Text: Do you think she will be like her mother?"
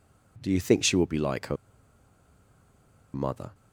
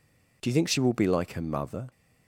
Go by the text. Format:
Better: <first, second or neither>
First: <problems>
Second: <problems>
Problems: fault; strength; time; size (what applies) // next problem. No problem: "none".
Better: second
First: pauses between "her" and "mother"; strong; at 1.5 s; 1.5 s long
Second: none